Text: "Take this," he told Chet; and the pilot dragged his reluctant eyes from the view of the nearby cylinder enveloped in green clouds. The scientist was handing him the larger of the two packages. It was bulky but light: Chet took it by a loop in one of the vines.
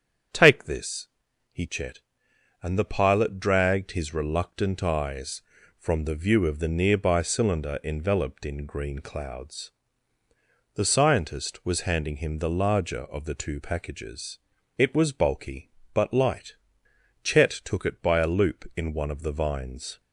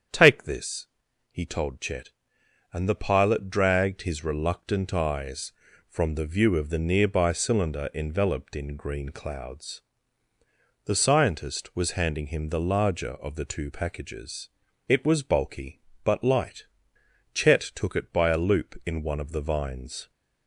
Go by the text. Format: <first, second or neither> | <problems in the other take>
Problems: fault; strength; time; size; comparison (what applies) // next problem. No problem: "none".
second | starts louder than the rest; strong; until 1.8 s; 8.5 dB; strong in the second // skips "told"; at 1.6 s